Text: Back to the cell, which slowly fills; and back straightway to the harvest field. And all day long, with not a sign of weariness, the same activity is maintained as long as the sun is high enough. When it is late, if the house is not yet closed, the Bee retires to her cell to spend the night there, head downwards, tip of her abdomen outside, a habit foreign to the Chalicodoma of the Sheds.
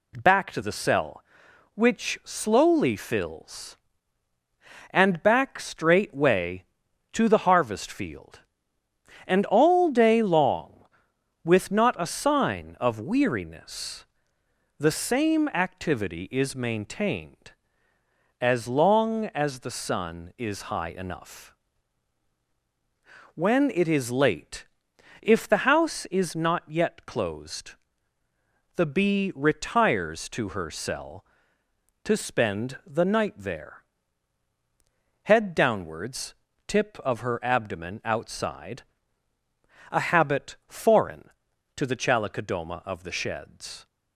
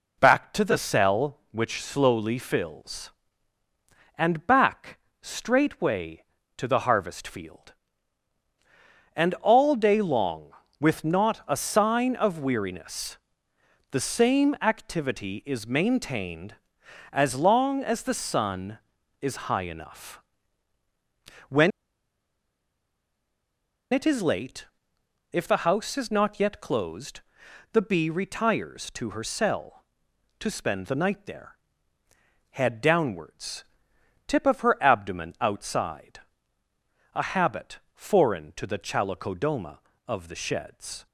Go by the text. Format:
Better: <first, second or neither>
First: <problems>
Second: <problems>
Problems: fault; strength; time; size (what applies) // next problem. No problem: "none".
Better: first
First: none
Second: pauses between "back" and "straightway"; slight; at 4.9 s; 0.22 s long // pauses between "When" and "it"; strong; at 21.7 s; 2.2 s long // pauses between "habit" and "foreign"; slight; at 37.7 s; 0.16 s long